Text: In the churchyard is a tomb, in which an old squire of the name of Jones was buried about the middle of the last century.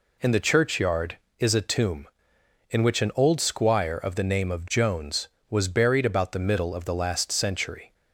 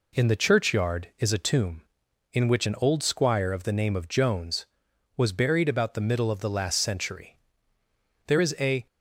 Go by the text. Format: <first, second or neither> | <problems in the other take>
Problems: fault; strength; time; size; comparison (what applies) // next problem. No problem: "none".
first | goes on to say "There is a"; from 8.2 s on; 0.60 s long